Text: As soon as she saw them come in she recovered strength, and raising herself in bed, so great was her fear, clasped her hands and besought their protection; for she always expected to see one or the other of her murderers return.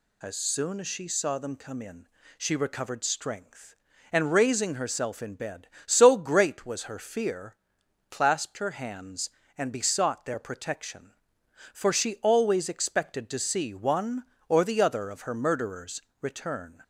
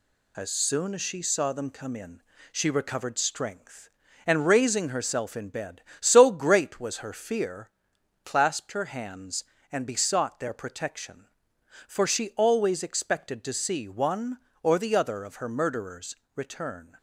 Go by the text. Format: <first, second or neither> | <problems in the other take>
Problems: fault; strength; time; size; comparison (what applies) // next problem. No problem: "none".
first | gets quieter; slight; throughout; 3 dB // pauses between "in" and "she"; slight; at 2.2 s; 0.32 s long; slight in the first // pauses between "murderers" and "return"; slight; at 16.1 s; 0.22 s long; slight in the first